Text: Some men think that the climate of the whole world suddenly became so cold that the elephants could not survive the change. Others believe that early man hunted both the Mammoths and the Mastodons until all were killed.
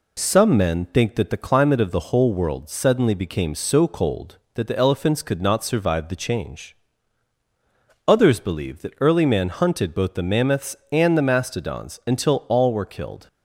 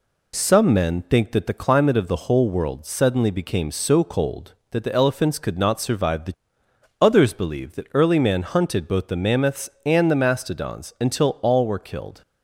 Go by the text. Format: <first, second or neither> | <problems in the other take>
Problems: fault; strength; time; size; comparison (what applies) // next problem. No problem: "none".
first | skips "change"; at 6.6 s